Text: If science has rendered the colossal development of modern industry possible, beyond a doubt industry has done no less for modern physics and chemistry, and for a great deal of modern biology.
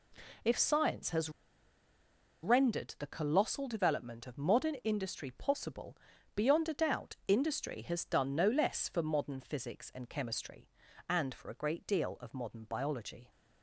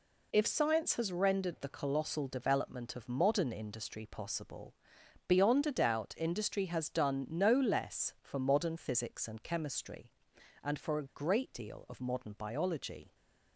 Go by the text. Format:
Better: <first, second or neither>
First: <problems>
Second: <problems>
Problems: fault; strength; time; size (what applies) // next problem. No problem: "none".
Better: second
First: pauses between "has" and "rendered"; at 1.2 s; 1.1 s long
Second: none